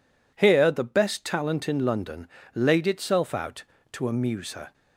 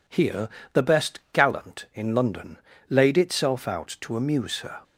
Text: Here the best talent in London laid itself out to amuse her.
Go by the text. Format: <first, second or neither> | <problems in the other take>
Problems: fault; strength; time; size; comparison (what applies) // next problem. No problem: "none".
first | pauses between "Here" and "the"; slight; at 0.4 s; 0.24 s long // says "gallant" for "talent"; at 1.3 s // pauses between "London" and "laid"; slight; at 2.5 s; 0.32 s long; slight in the first